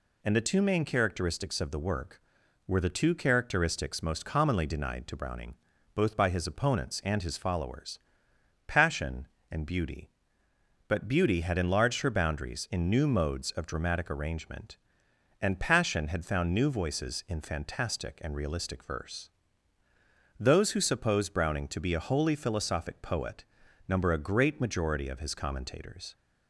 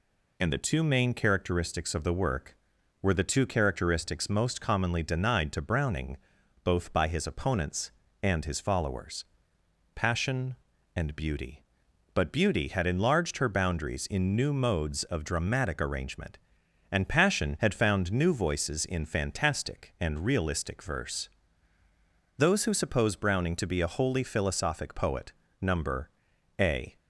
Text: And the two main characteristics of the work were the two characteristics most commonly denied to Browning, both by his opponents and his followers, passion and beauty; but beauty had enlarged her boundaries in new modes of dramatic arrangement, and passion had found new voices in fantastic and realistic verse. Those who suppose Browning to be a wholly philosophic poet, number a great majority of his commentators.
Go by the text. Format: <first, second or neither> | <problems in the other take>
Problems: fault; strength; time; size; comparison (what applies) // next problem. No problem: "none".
first | pauses between "number" and "a"; noticeable; at 26.0 s; 0.50 s long // stops before "great majority of his commentators"; at 26.9 s